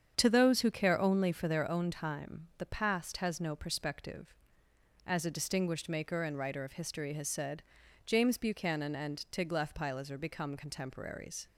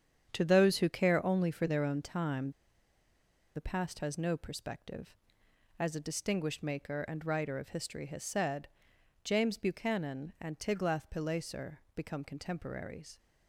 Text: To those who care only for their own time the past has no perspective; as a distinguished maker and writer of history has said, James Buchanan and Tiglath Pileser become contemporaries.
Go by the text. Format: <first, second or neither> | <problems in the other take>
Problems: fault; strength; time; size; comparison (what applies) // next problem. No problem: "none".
first | starts louder than the rest; strong; until 1.3 s; 8.5 dB; strong in the first // pauses between "time" and "the"; at 2.5 s; 1.0 s long // pauses between "Pileser" and "become"; slight; at 11.7 s; 0.16 s long